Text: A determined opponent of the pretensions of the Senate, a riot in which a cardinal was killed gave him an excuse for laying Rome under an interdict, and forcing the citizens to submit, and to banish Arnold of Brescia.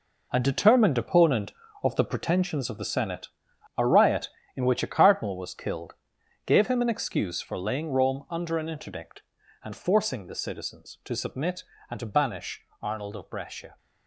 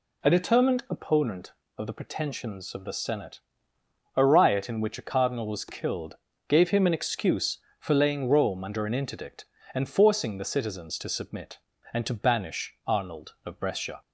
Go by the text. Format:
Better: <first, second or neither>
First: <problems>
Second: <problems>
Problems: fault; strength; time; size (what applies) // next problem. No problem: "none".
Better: second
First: gets quieter; strong; throughout; 11 dB // pauses between "killed" and "gave"; noticeable; at 5.9 s; 0.52 s long // pauses between "banish" and "Arnold"; slight; at 12.6 s; 0.18 s long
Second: pauses between "killed" and "gave"; slight; at 6.1 s; 0.32 s long